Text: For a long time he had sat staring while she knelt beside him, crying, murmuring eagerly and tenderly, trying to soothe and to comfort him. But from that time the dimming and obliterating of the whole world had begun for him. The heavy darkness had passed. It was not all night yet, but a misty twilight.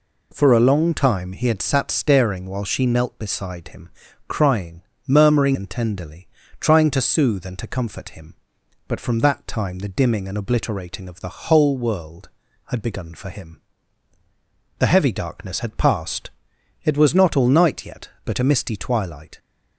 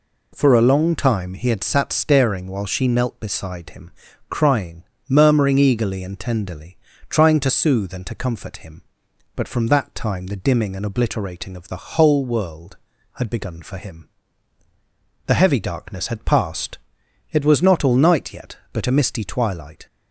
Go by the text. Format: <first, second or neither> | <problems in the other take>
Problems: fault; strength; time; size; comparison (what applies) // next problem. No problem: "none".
second | skips "eagerly"; at 5.5 s